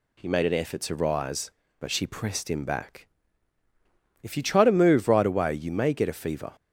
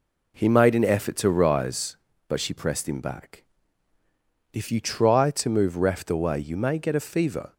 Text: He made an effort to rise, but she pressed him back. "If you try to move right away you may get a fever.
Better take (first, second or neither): first